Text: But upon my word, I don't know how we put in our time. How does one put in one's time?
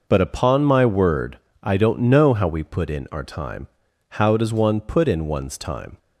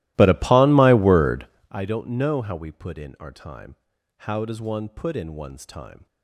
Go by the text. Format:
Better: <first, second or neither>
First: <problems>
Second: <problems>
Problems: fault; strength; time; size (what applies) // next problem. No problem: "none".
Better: first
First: none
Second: starts louder than the rest; strong; until 1.8 s; 16.5 dB